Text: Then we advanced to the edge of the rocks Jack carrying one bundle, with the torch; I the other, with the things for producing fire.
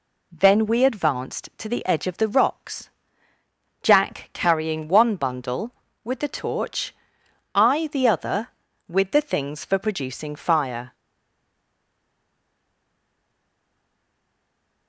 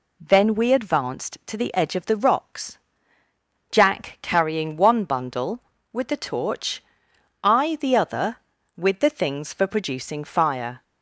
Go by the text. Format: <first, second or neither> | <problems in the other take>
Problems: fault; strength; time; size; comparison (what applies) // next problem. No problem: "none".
second | pauses between "rocks" and "Jack"; noticeable; at 2.8 s; 0.94 s long; noticeable in the second // stays silent after the last word; strong; from 10.9 s on; 3.9 s long